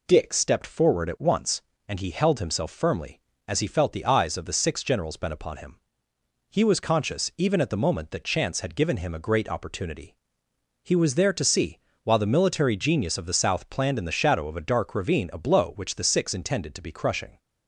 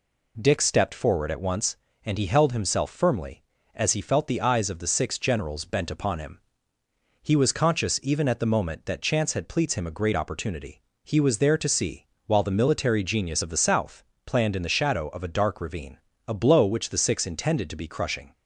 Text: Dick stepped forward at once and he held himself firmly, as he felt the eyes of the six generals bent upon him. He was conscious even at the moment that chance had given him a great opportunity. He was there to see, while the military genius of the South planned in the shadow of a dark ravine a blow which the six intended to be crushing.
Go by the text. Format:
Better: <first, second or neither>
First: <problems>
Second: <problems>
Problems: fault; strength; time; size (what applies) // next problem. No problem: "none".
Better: first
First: none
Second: says "pleats" for "given"; at 9.4 s // pauses between "South" and "planned"; slight; at 14.0 s; 0.22 s long // pauses between "ravine" and "a"; slight; at 15.9 s; 0.30 s long